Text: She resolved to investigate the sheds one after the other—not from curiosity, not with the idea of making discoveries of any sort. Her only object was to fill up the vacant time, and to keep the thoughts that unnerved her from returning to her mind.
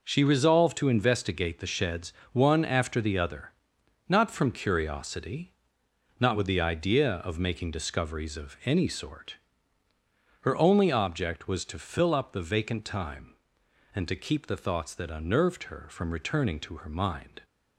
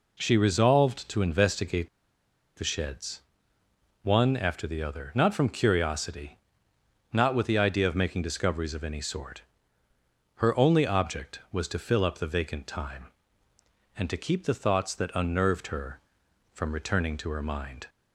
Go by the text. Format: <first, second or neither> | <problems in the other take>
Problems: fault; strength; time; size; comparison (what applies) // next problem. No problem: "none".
first | pauses between "investigate" and "the"; noticeable; at 1.8 s; 0.69 s long // pauses between "sheds" and "one"; noticeable; at 3.1 s; 0.84 s long; slight in the first